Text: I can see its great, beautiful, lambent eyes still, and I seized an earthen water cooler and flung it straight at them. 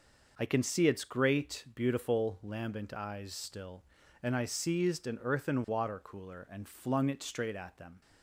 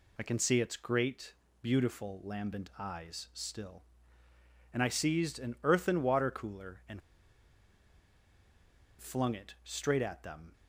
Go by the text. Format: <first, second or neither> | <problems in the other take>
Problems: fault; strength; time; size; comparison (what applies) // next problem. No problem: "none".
first | pauses between "and" and "flung"; strong; at 7.0 s; 2.0 s long